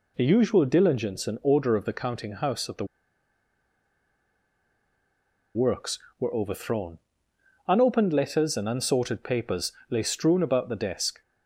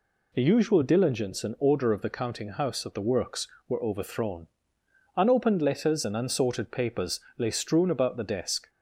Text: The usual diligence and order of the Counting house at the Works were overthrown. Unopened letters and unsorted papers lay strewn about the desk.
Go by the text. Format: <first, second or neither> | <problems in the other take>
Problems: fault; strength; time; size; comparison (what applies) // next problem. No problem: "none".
second | pauses between "the" and "Works"; strong; at 2.8 s; 2.6 s long // pauses between "papers" and "lay"; slight; at 9.7 s; 0.18 s long; slight in the second